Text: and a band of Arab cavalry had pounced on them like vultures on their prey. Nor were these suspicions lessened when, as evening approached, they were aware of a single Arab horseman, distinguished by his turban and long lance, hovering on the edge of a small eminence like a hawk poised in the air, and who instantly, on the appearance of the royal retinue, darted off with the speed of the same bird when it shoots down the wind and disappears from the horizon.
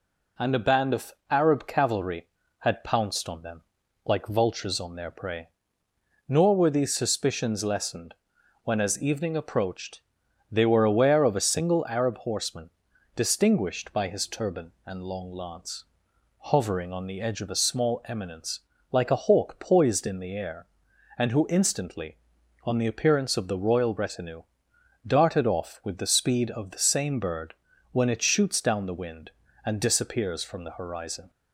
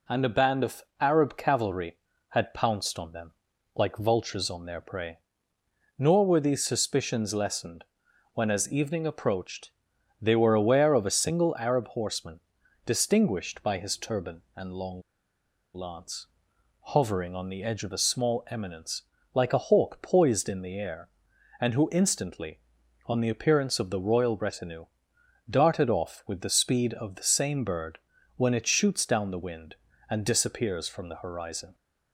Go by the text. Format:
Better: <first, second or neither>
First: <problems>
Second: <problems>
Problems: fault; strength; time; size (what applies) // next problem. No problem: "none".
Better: first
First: pauses between "of" and "Arab"; slight; at 1.1 s; 0.18 s long // pauses between "them" and "like"; at 3.6 s; 0.42 s long // pauses between "lessened" and "when"; noticeable; at 8.1 s; 0.48 s long // pauses between "eminence" and "like"; slight; at 18.6 s; 0.32 s long // pauses between "bird" and "when"; at 27.5 s; 0.38 s long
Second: pauses between "of" and "Arab"; slight; at 0.8 s; 0.18 s long // pauses between "them" and "like"; at 3.3 s; 0.42 s long // pauses between "lessened" and "when"; noticeable; at 7.8 s; 0.48 s long // pauses between "long" and "lance"; noticeable; at 15.0 s; 0.72 s long // pauses between "eminence" and "like"; slight; at 19.0 s; 0.32 s long // pauses between "bird" and "when"; at 27.9 s; 0.38 s long